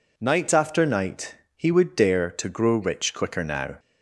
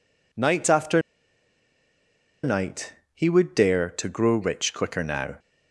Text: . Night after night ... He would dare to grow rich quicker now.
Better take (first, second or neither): first